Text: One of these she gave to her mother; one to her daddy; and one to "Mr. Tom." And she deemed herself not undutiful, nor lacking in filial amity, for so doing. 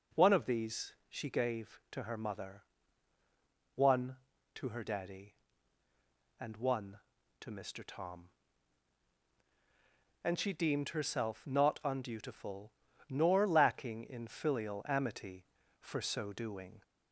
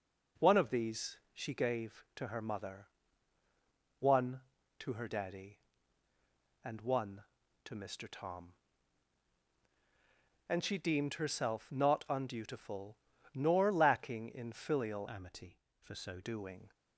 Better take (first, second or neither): first